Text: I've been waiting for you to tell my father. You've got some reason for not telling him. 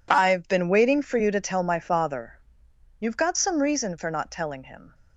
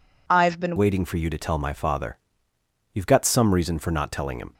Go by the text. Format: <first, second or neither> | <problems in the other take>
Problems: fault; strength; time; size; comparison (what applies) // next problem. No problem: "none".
first | changes voice at "waiting"; from 0.7 s on; 3.8 s long